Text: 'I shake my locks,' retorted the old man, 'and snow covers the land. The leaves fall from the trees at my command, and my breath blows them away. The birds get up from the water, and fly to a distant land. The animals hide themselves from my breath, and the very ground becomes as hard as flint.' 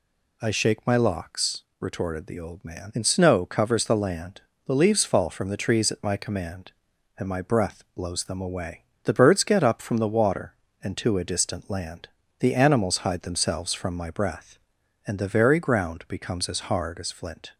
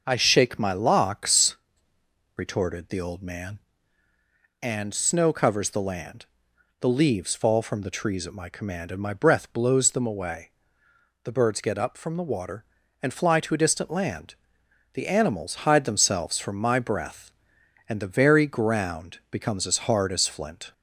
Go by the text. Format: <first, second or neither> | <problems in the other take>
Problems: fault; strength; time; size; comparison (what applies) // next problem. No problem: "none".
second | skips "fly"; at 10.9 s